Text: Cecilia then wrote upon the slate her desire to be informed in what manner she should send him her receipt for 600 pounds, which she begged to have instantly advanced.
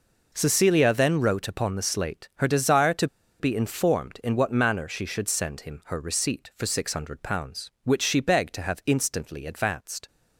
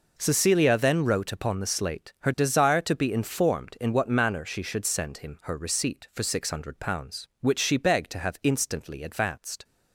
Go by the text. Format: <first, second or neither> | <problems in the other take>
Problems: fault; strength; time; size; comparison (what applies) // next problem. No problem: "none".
second | pauses between "to" and "be"; slight; at 3.0 s; 0.33 s long